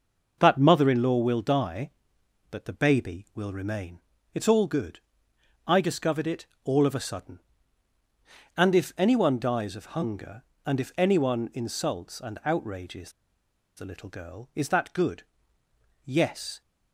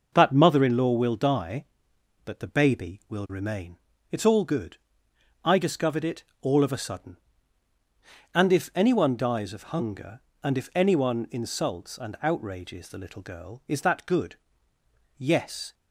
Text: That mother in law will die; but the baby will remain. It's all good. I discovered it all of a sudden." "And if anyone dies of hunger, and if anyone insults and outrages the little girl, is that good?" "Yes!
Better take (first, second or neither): second